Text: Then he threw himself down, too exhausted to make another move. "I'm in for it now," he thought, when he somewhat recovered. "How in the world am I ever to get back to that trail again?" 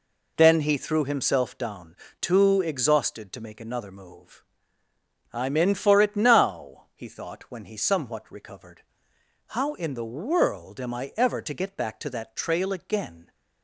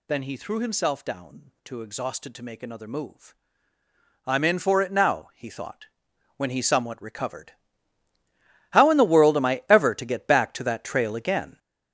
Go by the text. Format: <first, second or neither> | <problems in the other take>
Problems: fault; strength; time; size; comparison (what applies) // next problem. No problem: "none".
first | gets louder; strong; throughout; 8.5 dB